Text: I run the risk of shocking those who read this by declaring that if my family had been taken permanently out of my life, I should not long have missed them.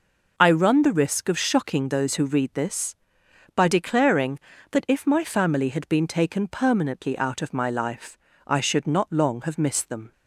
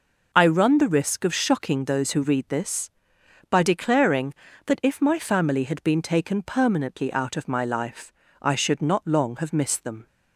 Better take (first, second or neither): neither